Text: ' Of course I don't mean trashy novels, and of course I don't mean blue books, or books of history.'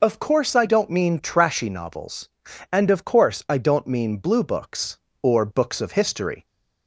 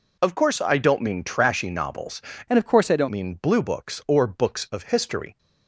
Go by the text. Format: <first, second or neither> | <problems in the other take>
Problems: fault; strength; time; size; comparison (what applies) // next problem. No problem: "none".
first | changes voice from "and" to "don't"; from 2.4 to 3.0 s; 0.6 s long